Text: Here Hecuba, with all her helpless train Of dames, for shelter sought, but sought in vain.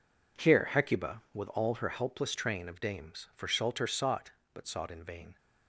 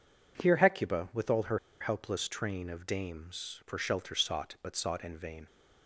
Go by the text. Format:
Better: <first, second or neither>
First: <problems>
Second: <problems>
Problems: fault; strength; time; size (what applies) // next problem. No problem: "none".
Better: first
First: none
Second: pauses between "her" and "helpless"; slight; at 1.5 s; 0.23 s long